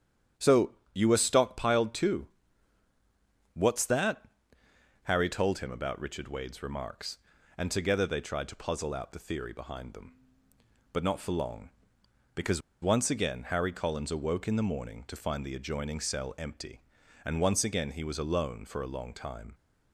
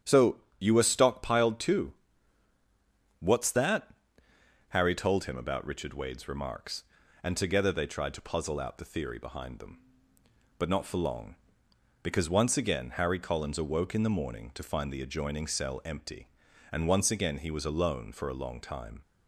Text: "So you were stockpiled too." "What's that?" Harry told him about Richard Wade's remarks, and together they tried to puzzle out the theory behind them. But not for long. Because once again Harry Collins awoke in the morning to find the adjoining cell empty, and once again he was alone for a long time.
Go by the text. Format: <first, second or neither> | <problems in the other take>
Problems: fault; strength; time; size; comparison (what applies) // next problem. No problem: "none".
second | starts louder than the rest; strong; until 1.5 s; 9.5 dB; strong in the second // pauses between "So" and "you"; slight; at 0.7 s; 0.18 s long; slight in the second // pauses between "Because" and "once"; slight; at 12.6 s; 0.21 s long